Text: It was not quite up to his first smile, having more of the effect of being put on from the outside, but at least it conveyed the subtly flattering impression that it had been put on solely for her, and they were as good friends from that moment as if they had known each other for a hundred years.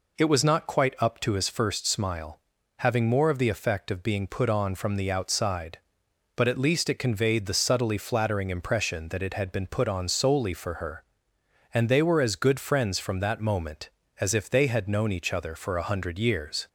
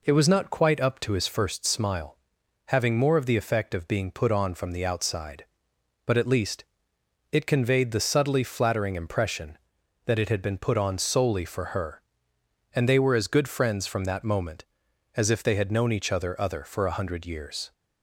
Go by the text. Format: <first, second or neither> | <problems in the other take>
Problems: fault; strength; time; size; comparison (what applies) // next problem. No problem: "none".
first | pauses between "least" and "it"; noticeable; at 6.6 s; 0.66 s long // says "other" twice; at 16.4 s